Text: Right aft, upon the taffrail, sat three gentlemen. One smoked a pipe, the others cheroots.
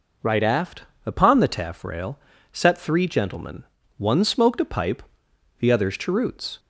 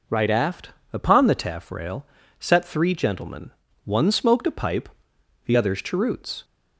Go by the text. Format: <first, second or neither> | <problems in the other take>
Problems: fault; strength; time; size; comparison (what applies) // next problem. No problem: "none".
neither | none